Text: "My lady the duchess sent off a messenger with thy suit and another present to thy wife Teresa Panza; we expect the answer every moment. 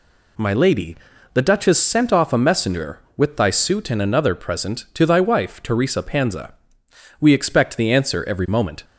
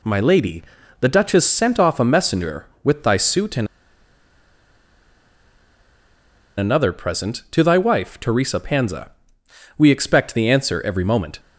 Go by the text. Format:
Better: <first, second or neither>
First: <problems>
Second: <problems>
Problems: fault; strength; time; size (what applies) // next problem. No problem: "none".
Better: first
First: pauses between "lady" and "the"; slight; at 0.9 s; 0.36 s long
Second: pauses between "lady" and "the"; slight; at 0.6 s; 0.36 s long // pauses between "and" and "another"; strong; at 3.6 s; 2.9 s long